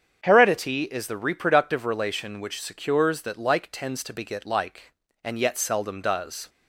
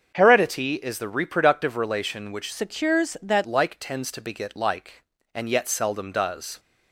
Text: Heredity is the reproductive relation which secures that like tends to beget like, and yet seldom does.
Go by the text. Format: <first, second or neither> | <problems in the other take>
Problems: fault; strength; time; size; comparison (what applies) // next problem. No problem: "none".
first | starts louder than the rest; until 1.1 s; 7 dB; strong in the first // changes voice from "secures" to "that"; from 2.5 to 3.4 s; 0.9 s long